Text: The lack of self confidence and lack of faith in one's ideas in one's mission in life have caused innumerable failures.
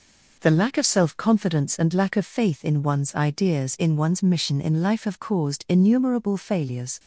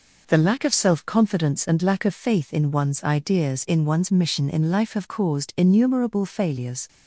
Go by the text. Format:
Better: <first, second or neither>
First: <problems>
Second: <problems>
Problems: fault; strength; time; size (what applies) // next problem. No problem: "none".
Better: neither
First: none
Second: none